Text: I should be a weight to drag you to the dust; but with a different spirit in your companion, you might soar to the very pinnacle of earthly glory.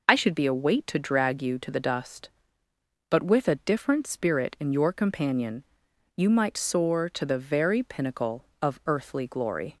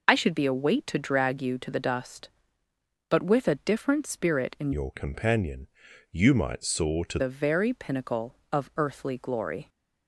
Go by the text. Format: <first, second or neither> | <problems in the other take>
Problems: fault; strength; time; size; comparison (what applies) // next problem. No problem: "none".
first | changes voice from "your" to "to"; from 4.7 to 7.1 s; 2.4 s long